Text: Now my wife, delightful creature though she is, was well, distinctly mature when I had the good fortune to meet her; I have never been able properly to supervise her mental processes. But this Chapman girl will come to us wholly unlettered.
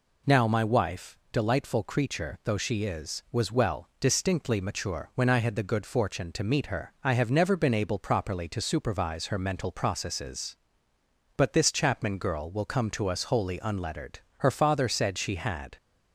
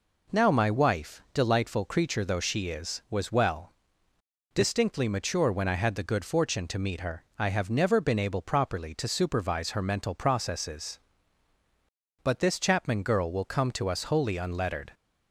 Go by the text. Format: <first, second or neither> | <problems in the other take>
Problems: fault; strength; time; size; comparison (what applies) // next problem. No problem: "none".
second | goes on to say "Her father said she had"; from 14.3 s on; 1.3 s long